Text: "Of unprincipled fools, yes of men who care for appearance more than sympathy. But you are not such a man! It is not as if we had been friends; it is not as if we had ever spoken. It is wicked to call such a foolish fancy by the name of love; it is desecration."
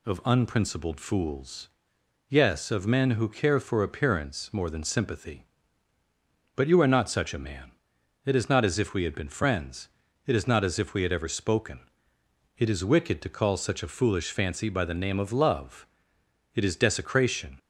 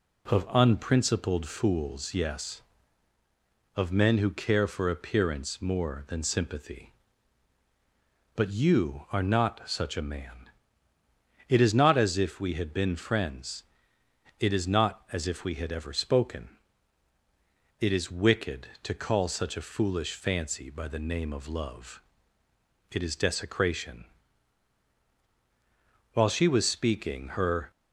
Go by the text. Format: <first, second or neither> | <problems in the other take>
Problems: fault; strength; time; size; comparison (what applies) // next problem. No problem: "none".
first | goes on to say "While she was speaking her"; from 26.1 s on; 1.5 s long